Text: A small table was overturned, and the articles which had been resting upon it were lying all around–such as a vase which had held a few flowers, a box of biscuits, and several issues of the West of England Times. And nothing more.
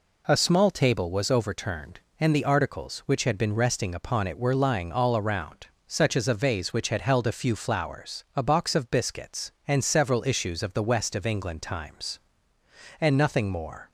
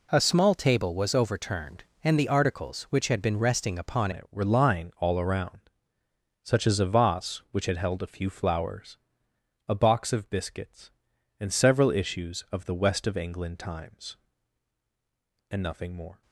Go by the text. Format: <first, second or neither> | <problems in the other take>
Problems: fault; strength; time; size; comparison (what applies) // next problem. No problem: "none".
first | changes voice at "it"; from 4.1 s on; 12.1 s long